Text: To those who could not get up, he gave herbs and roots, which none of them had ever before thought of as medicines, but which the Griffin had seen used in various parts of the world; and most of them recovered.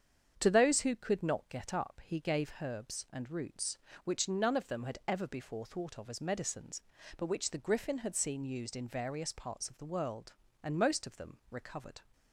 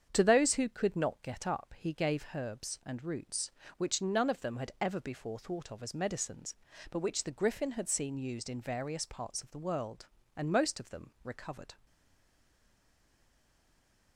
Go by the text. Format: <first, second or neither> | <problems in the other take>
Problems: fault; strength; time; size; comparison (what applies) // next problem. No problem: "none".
first | starts louder than the rest; strong; until 1.1 s; 8 dB; strong in the first // stays silent after the last word; from 11.8 s on; 2.3 s long